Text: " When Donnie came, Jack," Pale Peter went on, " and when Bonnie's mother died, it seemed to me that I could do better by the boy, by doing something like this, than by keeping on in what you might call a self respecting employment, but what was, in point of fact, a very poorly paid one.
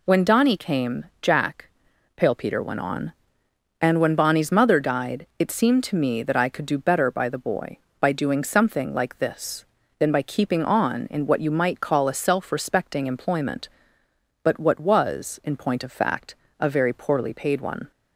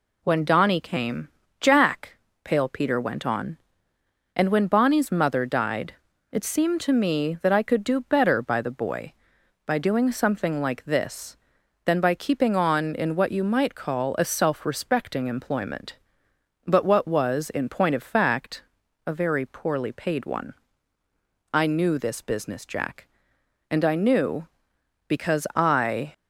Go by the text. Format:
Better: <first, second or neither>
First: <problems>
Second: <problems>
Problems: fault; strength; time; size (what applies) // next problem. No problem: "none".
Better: first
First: none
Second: goes on to say "I knew this business Jack and I knew because I"; strong; from 21.5 s on; 4.6 s long